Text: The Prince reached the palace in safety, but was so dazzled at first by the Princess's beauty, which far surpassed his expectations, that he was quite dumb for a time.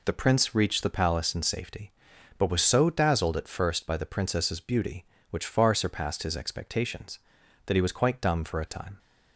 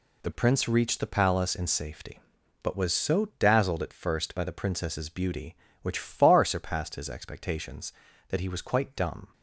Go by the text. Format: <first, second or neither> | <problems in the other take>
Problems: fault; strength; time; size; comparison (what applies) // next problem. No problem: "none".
first | stops before "for a time"; at 9.3 s